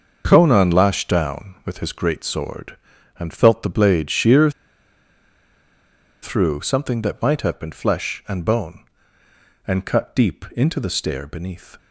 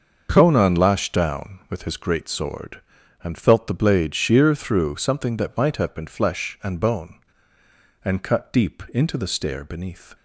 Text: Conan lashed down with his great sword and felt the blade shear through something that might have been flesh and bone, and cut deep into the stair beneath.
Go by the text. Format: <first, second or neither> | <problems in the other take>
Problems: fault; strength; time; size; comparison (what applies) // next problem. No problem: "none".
second | starts louder than the rest; until 1.2 s; 6.5 dB; also in the second // pauses between "shear" and "through"; strong; at 4.4 s; 1.7 s long